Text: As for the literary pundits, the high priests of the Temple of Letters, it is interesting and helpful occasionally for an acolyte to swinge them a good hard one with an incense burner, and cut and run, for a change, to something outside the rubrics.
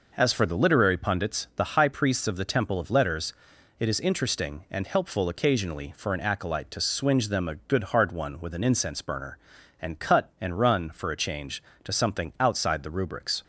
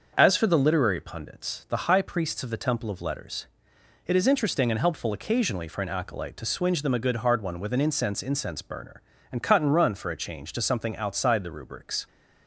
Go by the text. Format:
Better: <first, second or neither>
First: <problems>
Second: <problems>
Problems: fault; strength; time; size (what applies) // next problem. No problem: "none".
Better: first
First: none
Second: starts louder than the rest; until 1.1 s; 6.5 dB // says "incense" twice; at 8.2 s